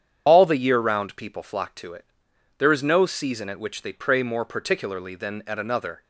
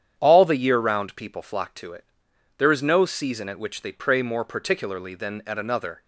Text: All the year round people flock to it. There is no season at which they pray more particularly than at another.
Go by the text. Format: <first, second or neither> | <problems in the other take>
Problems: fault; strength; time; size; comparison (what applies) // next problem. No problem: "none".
second | loses the start of "All"; at 0.2 s; 75 ms // starts louder than the rest; strong; until 1.2 s; 8.5 dB; strong in the second